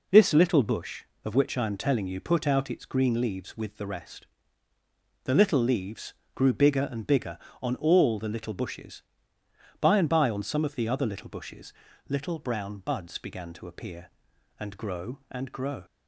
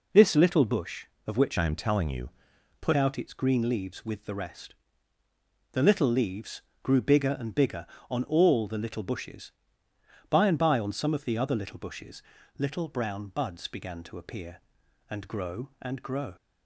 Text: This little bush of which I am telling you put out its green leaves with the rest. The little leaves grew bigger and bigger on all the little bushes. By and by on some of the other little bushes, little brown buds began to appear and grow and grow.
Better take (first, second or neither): first